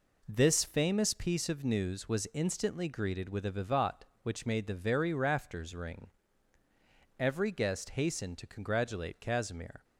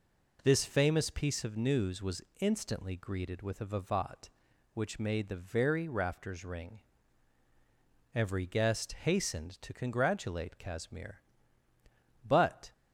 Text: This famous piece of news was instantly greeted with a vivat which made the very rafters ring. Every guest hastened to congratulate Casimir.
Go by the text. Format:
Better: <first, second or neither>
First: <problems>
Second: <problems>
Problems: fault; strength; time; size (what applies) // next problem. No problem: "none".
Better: first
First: none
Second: pauses between "was" and "instantly"; slight; at 2.2 s; 0.18 s long // goes on to say "But"; slight; from 12.2 s on; 0.46 s long